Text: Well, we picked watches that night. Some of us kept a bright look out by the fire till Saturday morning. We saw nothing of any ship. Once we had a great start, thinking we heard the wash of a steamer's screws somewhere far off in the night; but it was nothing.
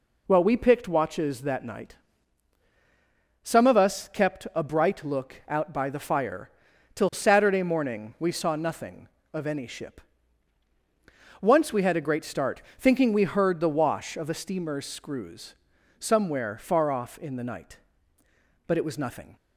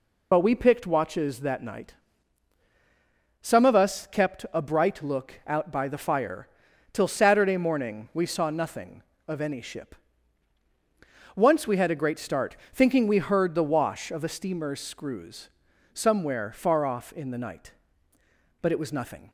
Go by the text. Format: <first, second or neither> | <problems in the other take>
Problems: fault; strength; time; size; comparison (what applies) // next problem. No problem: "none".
first | loses the start of "Well"; at 0.3 s; 50 ms // pauses between "fire" and "till"; noticeable; at 6.4 s; 0.46 s long; noticeable in the first // pauses between "screws" and "somewhere"; at 15.4 s; 0.42 s long; also in the first